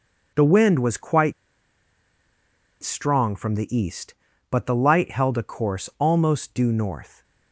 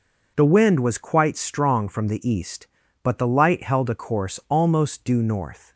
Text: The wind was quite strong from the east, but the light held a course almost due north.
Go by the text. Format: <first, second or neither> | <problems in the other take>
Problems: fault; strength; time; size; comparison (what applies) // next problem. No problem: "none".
second | pauses between "quite" and "strong"; strong; at 1.3 s; 1.4 s long